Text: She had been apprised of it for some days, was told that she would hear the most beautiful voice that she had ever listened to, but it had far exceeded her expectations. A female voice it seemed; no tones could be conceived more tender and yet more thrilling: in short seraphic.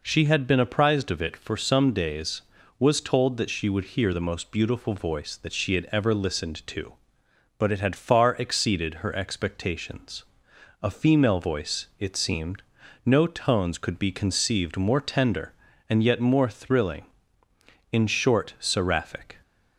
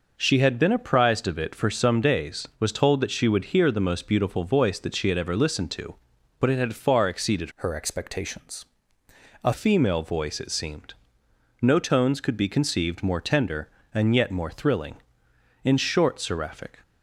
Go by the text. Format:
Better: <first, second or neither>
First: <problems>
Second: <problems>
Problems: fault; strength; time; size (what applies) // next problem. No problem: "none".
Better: first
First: none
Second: changes voice from "her" to "A"; from 7.5 to 9.5 s; 2.0 s long